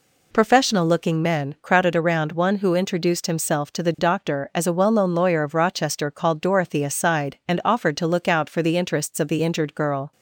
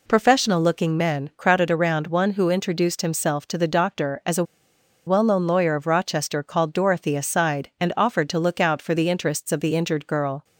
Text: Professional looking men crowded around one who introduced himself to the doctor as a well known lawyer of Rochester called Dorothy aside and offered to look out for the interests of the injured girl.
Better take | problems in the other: first | pauses between "a" and "well"; noticeable; at 4.4 s; 0.63 s long

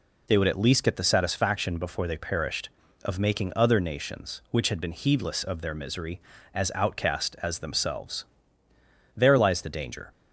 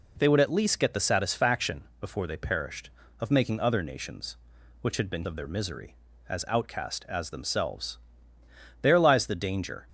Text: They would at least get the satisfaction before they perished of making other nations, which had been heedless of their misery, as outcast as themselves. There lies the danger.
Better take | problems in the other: first | pauses between "satisfaction" and "before"; slight; at 1.8 s; 0.16 s long // skips "heedless"; at 5.2 s

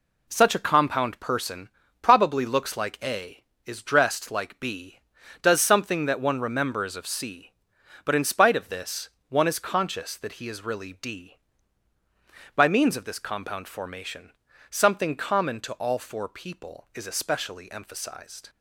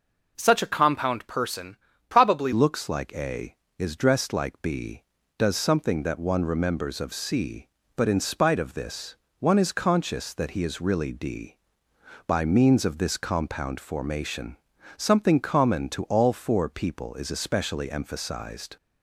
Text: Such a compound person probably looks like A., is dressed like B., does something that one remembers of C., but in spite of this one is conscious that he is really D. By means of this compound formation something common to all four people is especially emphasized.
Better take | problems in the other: first | pauses between "person" and "probably"; slight; at 1.7 s; 0.34 s long; slight in the first // changes voice at "looks"; from 2.5 s on; 16.2 s long // pauses between "this" and "one"; slight; at 9.1 s; 0.24 s long; slight in the first // pauses between "formation" and "something"; at 14.5 s; 0.40 s long; also in the first

